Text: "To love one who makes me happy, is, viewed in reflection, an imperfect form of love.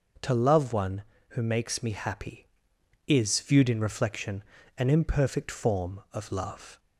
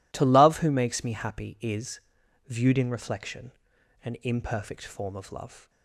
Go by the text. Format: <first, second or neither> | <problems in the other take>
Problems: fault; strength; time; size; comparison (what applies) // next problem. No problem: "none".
first | skips "one"; at 0.5 s